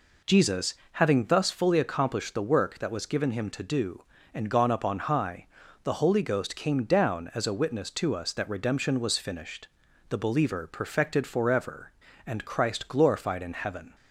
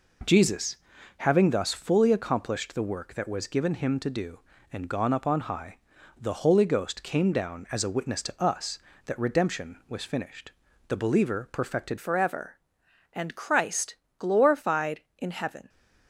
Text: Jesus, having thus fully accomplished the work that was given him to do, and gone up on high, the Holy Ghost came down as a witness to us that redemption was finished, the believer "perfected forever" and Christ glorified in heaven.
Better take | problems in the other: first | changes voice at "forever"; from 11.9 s on; 3.7 s long // pauses between "Christ" and "glorified"; slight; at 13.9 s; 0.22 s long

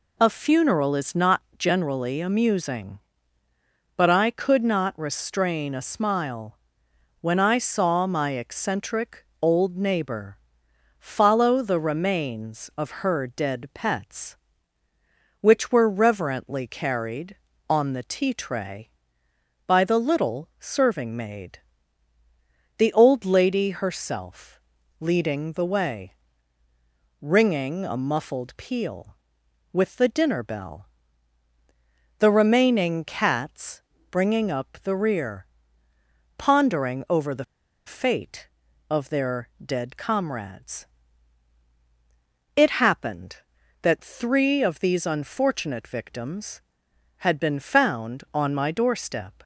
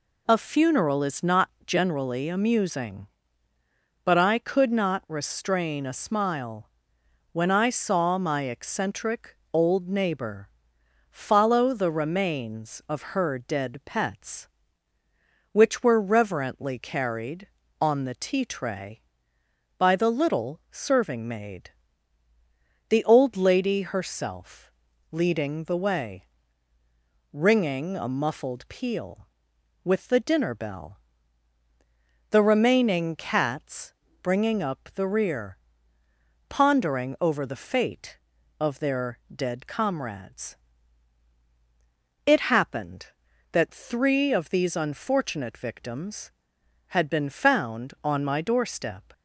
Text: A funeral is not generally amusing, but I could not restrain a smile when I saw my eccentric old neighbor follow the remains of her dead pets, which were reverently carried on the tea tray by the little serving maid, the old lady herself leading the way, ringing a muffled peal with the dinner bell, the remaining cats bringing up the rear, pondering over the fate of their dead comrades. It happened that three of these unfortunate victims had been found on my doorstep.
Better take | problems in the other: second | pauses between "not" and "generally"; slight; at 1.4 s; 0.18 s long; slight in the second // pauses between "smile" and "when"; noticeable; at 6.5 s; 0.64 s long; noticeable in the second // pauses between "eccentric" and "old"; slight; at 9.2 s; 0.18 s long; slight in the second // pauses between "neighbor" and "follow"; noticeable; at 10.3 s; 0.62 s long; noticeable in the second // pauses between "herself" and "leading"; at 24.5 s; 0.40 s long; also in the second // pauses between "cats" and "bringing"; slight; at 33.8 s; 0.28 s long; slight in the second // pauses between "the" and "fate"; at 37.4 s; 0.41 s long // pauses between "their" and "dead"; slight; at 39.4 s; 0.18 s long; slight in the second

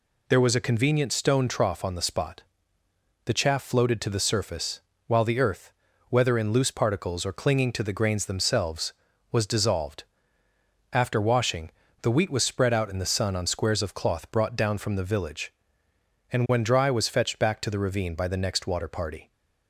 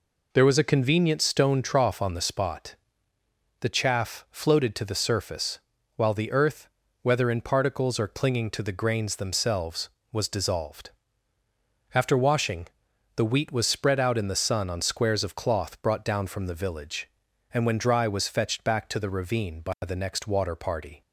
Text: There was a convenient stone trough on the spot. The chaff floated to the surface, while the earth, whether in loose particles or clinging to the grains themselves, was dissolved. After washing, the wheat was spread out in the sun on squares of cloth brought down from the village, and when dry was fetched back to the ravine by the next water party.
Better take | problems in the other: first | skips "loose"; at 7.4 s

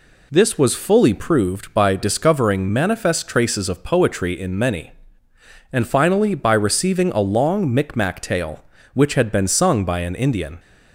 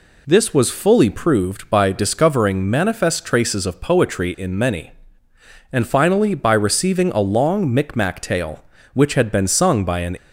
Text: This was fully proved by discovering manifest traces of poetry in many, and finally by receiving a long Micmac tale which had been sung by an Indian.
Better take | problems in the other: first | stops before "Indian"; at 10.1 s

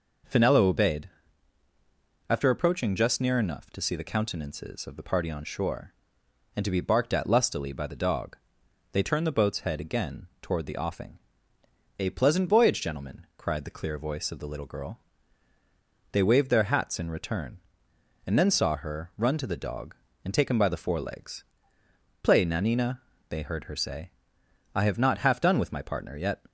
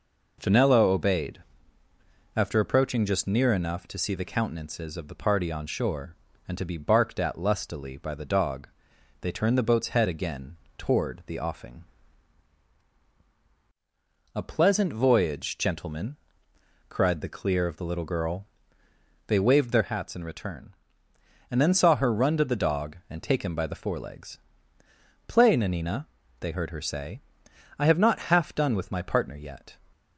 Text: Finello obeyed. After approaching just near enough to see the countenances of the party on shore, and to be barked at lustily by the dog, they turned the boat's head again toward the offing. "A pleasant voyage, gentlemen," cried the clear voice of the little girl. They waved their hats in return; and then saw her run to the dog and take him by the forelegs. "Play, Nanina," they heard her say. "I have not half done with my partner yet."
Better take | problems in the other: first | pauses between "again" and "toward"; slight; at 10.5 s; 0.22 s long // skips "voice"; at 17.6 s

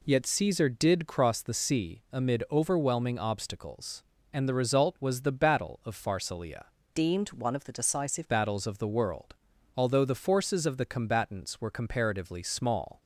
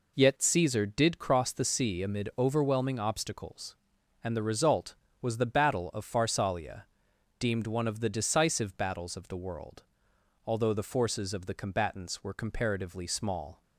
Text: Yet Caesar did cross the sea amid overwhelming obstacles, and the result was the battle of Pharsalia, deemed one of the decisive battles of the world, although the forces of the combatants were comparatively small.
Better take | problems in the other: second | changes voice from "deemed" to "decisive"; from 6.9 to 8.2 s; 1.3 s long

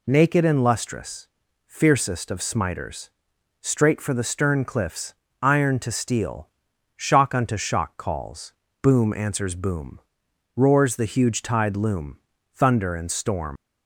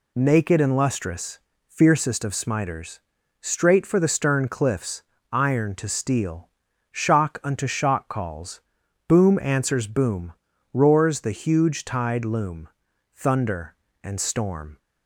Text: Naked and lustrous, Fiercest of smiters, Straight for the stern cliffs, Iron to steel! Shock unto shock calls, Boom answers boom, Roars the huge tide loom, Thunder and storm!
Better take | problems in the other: second | leaves "storm" unfinished; at 13.5 s; 60 ms

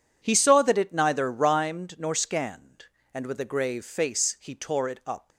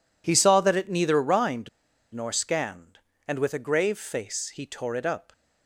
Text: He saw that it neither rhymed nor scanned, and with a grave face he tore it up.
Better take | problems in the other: first | pauses between "rhymed" and "nor"; at 1.6 s; 0.45 s long

